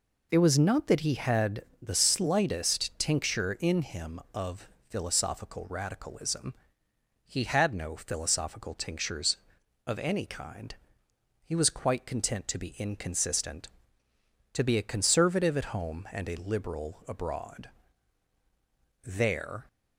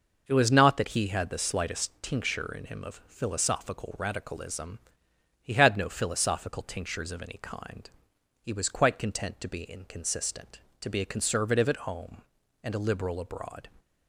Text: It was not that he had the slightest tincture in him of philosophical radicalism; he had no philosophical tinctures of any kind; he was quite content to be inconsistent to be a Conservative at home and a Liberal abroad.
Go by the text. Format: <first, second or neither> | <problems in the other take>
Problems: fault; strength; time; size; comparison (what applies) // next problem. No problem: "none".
second | pauses between "had" and "the"; slight; at 1.6 s; 0.18 s long // pauses between "of" and "philosophical"; slight; at 4.6 s; 0.20 s long // goes on to say "There"; noticeable; from 19.0 s on; 0.64 s long